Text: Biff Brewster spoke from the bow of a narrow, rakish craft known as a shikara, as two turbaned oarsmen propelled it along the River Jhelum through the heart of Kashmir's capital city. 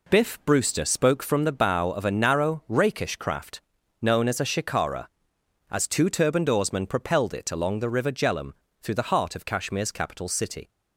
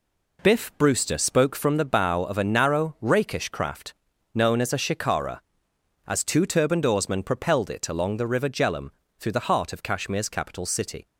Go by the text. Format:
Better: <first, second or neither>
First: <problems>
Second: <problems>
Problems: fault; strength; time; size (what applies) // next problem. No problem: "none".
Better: neither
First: pauses between "craft" and "known"; at 3.5 s; 0.42 s long // pauses between "Jhelum" and "through"; slight; at 8.5 s; 0.28 s long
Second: pauses between "craft" and "known"; at 3.9 s; 0.42 s long // pauses between "Jhelum" and "through"; slight; at 8.8 s; 0.28 s long